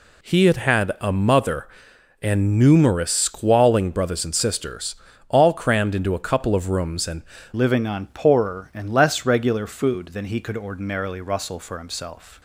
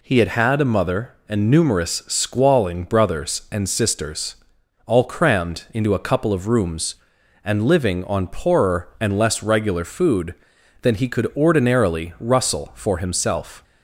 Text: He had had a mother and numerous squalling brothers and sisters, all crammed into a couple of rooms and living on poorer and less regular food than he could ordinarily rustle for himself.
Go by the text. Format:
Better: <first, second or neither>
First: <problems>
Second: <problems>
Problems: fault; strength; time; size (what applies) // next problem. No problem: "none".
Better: second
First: changes voice at "living"; from 7.5 s on; 4.9 s long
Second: none